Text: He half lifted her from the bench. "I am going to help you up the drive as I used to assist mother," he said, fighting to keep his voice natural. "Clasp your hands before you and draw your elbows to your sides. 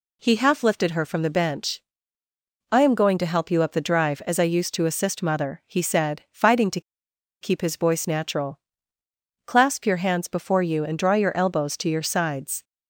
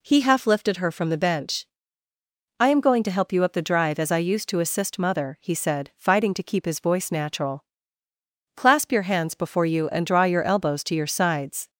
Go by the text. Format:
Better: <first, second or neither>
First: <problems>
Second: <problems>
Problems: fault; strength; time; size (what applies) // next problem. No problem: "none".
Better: second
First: pauses between "to" and "keep"; noticeable; at 6.8 s; 0.59 s long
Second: none